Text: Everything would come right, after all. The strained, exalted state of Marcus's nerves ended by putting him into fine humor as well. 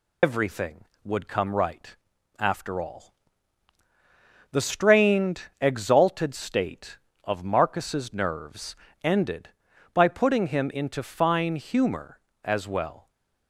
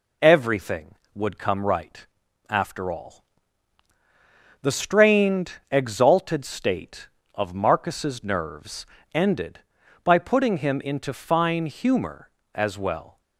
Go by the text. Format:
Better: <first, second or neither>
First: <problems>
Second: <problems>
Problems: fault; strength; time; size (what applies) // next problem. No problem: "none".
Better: second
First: loses the start of "Everything"; at 0.2 s; 115 ms // pauses between "nerves" and "ended"; slight; at 8.7 s; 0.30 s long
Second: pauses between "nerves" and "ended"; slight; at 8.8 s; 0.30 s long